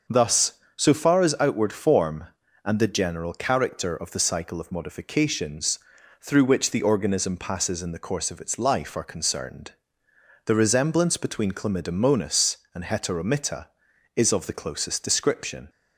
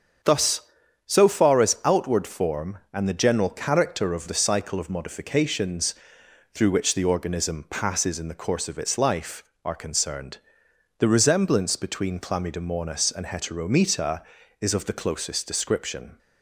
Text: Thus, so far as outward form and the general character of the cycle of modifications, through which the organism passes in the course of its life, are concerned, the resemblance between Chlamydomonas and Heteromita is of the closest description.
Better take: neither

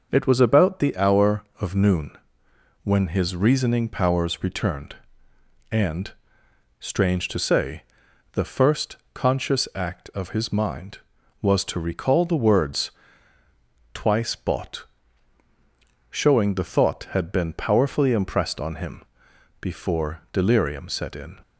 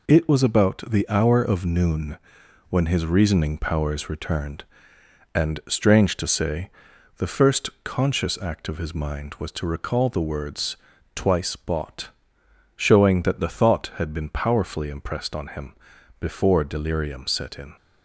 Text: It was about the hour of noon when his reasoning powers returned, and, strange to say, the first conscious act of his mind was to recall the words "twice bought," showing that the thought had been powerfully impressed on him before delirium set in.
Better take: second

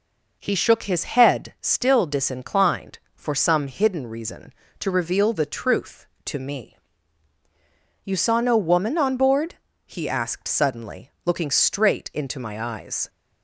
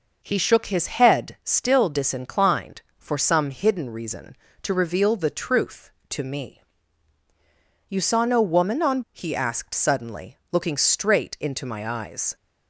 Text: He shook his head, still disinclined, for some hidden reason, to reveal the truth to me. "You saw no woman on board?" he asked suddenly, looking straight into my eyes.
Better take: first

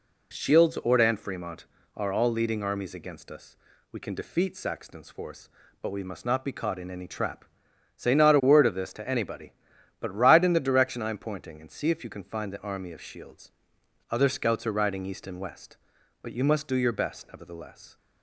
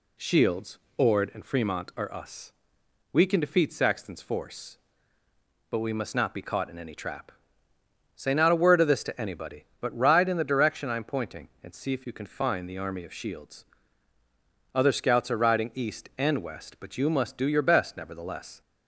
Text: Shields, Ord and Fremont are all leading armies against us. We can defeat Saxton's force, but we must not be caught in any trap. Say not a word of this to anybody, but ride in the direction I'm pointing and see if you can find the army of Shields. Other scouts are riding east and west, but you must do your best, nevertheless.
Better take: first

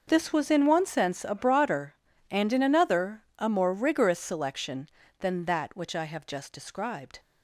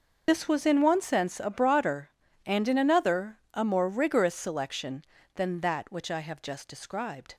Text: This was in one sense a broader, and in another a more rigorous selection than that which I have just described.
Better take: first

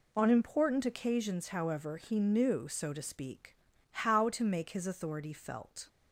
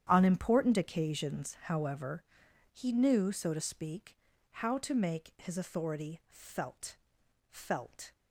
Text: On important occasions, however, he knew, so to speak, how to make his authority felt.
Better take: first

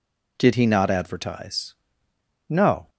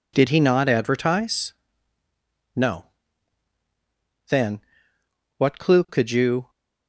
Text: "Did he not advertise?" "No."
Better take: first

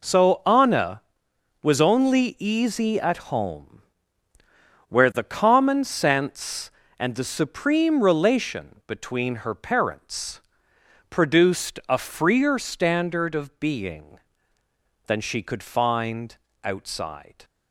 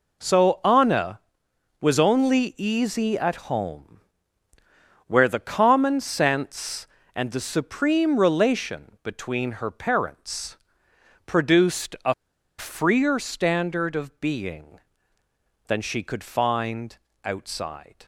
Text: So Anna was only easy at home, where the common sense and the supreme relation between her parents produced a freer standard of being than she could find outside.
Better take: first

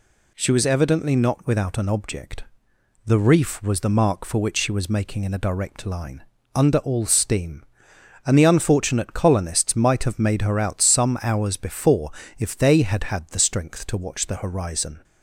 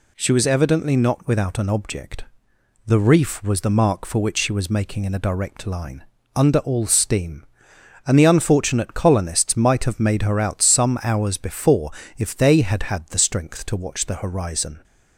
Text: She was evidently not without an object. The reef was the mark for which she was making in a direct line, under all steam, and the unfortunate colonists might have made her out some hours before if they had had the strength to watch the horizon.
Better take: neither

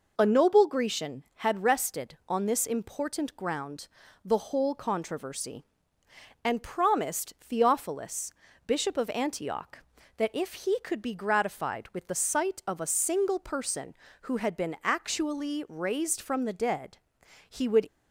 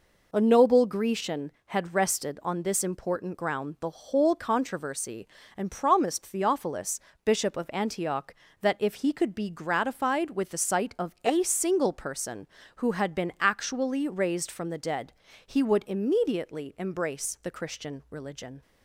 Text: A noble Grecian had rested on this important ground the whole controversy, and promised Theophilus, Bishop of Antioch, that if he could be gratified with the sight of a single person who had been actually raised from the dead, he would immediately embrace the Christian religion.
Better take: second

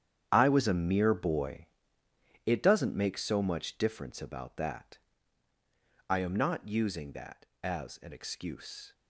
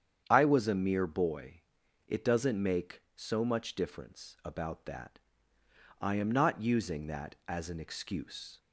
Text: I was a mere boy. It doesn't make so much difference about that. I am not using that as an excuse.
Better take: second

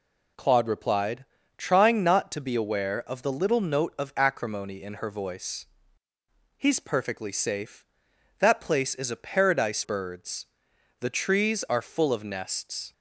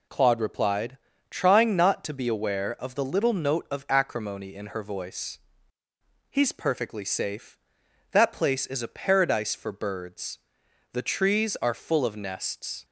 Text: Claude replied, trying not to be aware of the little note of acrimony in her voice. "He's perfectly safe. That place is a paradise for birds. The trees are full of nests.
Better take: second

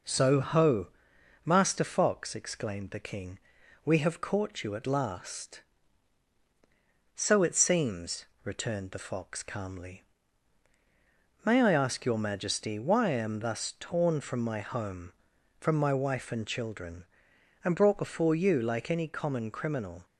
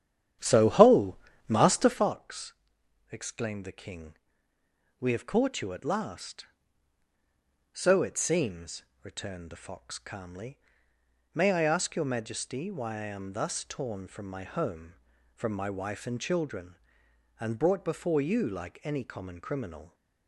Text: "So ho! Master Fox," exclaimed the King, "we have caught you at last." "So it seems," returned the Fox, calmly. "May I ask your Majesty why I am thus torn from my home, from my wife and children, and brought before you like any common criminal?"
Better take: first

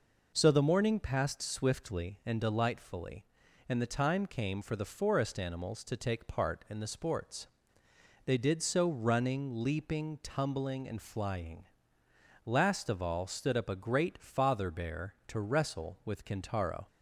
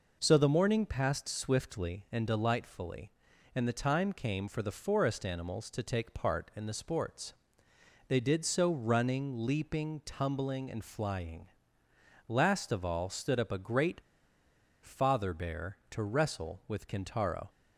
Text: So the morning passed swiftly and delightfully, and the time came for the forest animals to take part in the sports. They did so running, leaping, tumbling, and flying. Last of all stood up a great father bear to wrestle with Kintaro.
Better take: first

